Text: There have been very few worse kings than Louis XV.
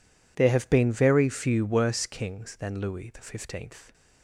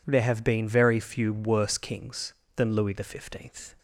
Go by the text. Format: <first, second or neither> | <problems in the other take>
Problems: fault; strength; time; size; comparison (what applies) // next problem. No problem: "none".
neither | none